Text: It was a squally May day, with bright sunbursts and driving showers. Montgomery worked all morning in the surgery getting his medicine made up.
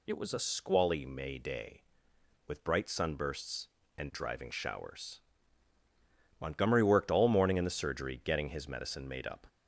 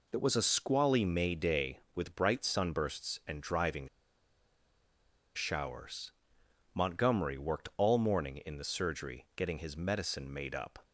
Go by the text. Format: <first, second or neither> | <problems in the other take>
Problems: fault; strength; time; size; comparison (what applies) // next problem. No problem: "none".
first | pauses between "driving" and "showers"; strong; at 3.8 s; 1.4 s long